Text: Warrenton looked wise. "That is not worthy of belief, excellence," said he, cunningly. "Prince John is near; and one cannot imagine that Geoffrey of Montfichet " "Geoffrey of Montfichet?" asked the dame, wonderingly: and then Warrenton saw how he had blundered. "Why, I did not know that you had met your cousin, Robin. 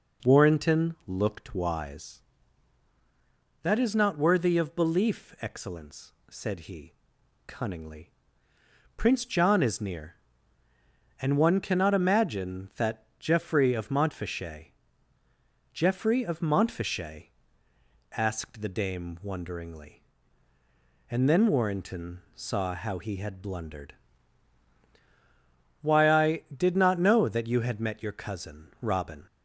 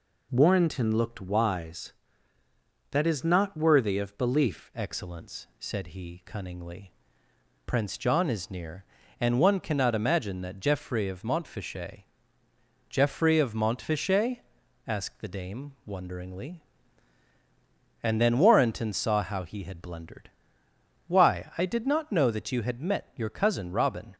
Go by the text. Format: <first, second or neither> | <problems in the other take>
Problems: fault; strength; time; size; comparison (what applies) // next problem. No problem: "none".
first | changes voice at "excellence"; from 4.7 s on; 19.4 s long